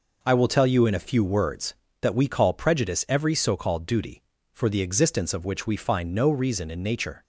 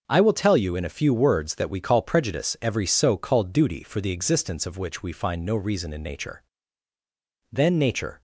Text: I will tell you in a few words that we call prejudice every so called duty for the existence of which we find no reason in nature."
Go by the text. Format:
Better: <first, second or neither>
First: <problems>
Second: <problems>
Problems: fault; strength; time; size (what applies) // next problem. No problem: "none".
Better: first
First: none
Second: starts louder than the rest; until 1.0 s; 6.5 dB // goes on to say "Then nature"; noticeable; from 7.5 s on; 0.70 s long